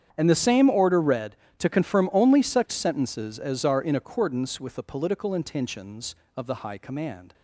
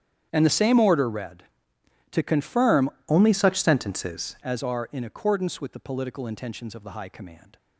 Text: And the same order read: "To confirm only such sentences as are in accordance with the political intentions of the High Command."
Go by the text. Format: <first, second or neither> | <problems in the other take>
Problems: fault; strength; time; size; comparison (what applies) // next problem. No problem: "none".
first | starts louder than the rest; strong; until 1.3 s; 9 dB; strong in the first // changes voice from "only" to "sentences"; from 3.0 to 4.3 s; 1.3 s long